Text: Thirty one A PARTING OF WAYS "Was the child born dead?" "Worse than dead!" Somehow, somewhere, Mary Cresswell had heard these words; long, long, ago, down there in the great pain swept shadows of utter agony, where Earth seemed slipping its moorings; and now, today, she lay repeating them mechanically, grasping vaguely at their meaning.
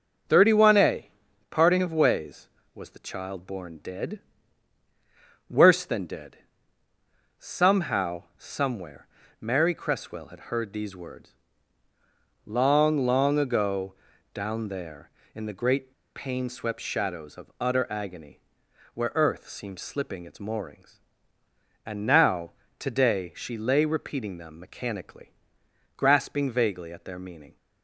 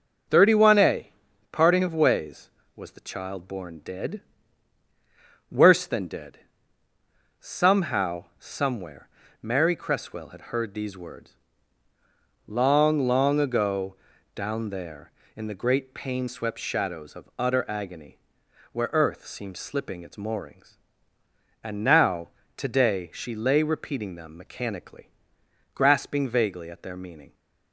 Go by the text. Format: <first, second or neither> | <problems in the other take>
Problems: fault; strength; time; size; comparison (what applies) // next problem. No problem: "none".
second | starts louder than the rest; noticeable; until 1.7 s; 6 dB; noticeable in the second // pauses between "A" and "PARTING"; at 1.0 s; 0.42 s long; also in the second // pauses between "great" and "pain"; slight; at 15.9 s; 0.23 s long